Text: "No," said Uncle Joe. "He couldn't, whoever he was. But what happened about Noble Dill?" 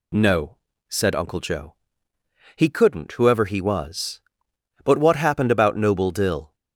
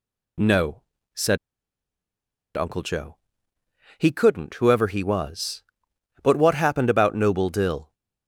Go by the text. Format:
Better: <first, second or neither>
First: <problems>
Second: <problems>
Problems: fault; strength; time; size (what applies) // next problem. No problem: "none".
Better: first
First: none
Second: pauses between "said" and "Uncle"; at 1.3 s; 1.1 s long